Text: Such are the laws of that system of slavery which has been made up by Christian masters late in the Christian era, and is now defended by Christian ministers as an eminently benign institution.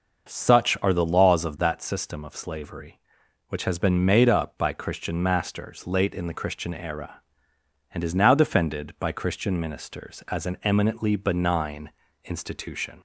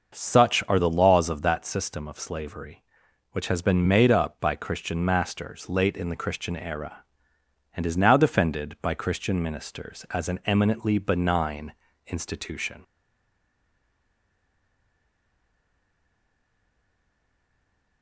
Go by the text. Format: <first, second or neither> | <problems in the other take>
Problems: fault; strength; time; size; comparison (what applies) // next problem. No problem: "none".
first | starts louder than the rest; noticeable; until 1.2 s; 6 dB; noticeable in the first // pauses between "benign" and "institution"; slight; at 11.7 s; 0.36 s long; slight in the first // stays silent after the last word; strong; from 12.8 s on; 5.2 s long